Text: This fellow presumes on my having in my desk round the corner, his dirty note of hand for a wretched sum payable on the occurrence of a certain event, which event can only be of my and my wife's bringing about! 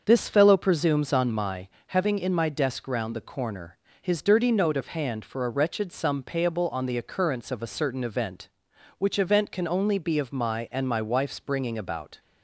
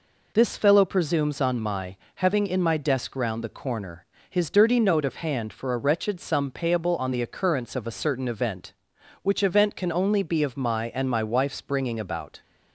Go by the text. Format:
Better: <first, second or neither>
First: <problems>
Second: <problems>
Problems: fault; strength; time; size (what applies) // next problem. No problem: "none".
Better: second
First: starts louder than the rest; until 1.5 s; 6.5 dB // pauses between "my" and "having"; slight; at 1.6 s; 0.18 s long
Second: pauses between "my" and "having"; slight; at 1.9 s; 0.18 s long